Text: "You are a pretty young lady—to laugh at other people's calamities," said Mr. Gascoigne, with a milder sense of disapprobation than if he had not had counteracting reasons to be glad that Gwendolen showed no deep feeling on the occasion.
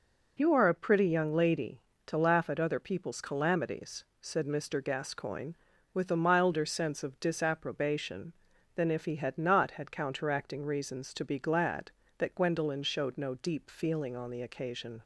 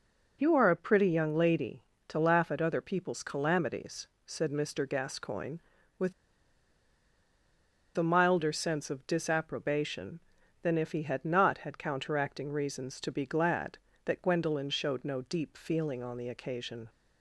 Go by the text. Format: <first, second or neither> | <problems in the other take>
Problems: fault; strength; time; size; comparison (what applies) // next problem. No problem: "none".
first | pauses between "with" and "a"; strong; at 6.1 s; 1.8 s long